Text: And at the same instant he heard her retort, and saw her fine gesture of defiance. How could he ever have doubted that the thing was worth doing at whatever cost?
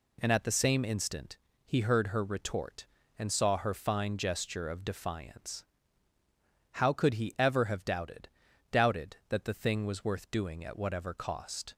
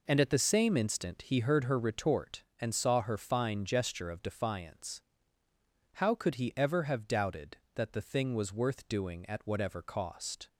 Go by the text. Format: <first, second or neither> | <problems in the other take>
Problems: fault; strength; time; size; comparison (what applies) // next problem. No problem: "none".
second | pauses between "instant" and "he"; slight; at 1.3 s; 0.28 s long // says "doubted" twice; at 8.7 s